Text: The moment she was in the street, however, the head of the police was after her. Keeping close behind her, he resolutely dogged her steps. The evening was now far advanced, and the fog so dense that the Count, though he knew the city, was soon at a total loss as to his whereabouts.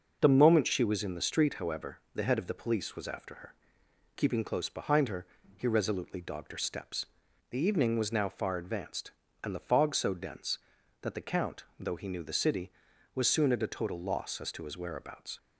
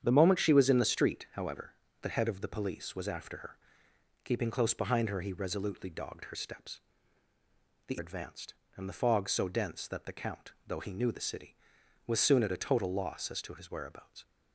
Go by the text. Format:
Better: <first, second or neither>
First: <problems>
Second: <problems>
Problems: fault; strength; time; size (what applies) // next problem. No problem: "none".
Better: first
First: none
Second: starts louder than the rest; strong; until 1.0 s; 8.5 dB // skips "evening was now far"; at 7.9 s